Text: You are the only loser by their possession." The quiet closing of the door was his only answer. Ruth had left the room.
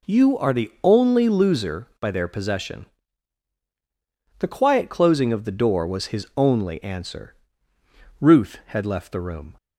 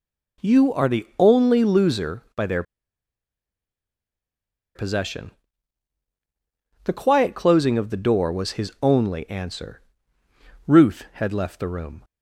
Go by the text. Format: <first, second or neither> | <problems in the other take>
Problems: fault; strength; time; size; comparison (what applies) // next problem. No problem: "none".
first | pauses between "their" and "possession"; strong; at 2.6 s; 2.1 s long